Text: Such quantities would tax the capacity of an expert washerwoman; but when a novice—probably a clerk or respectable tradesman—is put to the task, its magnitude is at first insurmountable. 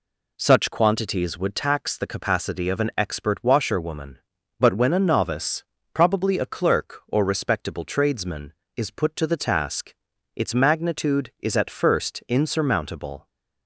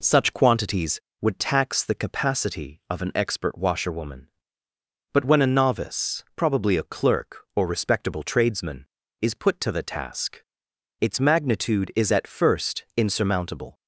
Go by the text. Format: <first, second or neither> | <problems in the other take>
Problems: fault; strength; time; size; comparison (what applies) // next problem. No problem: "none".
neither | none